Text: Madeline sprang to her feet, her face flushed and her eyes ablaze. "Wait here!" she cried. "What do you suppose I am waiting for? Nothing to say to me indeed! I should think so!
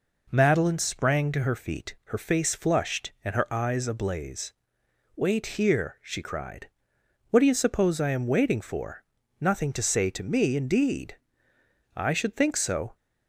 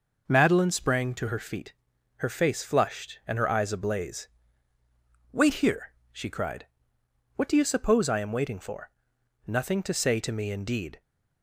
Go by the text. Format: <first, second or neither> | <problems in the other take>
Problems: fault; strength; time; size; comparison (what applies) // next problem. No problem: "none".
first | stops before "I should think so"; at 11.0 s